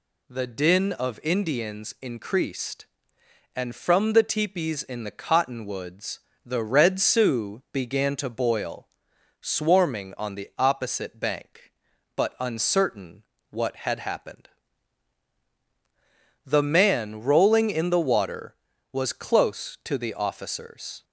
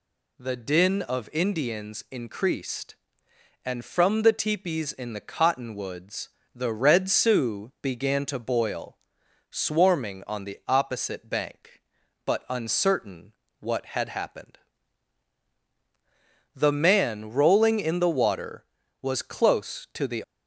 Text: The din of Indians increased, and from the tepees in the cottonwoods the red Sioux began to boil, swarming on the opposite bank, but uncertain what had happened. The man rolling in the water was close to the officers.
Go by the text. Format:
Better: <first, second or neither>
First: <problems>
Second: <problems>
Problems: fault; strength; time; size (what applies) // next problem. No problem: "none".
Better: first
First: pauses between "cottonwoods" and "the"; slight; at 6.1 s; 0.26 s long // pauses between "uncertain" and "what"; slight; at 13.2 s; 0.30 s long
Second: pauses between "cottonwoods" and "the"; slight; at 6.2 s; 0.26 s long // pauses between "uncertain" and "what"; slight; at 13.3 s; 0.30 s long // stops before "officers"; at 20.2 s